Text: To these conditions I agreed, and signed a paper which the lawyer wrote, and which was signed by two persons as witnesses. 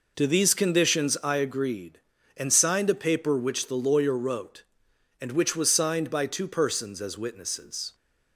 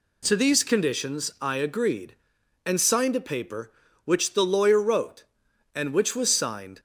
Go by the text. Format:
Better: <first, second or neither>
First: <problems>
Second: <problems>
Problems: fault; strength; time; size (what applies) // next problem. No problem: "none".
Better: first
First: none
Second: stops before "by two persons as witnesses"; at 6.7 s